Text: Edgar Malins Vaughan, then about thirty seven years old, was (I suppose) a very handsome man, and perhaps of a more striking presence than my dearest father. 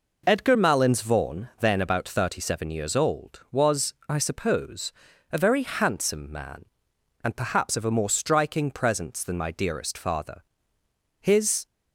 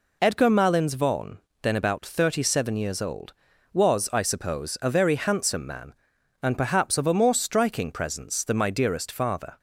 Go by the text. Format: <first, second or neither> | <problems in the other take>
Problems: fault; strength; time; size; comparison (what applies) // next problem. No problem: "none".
second | goes on to say "His"; slight; from 11.1 s on; 0.46 s long